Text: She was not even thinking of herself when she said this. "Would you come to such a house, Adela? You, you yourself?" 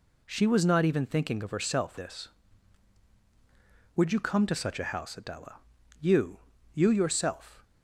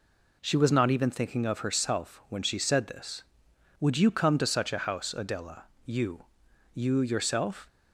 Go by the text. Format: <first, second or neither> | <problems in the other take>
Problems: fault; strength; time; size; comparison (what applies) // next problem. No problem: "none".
second | skips "when she said"; at 1.9 s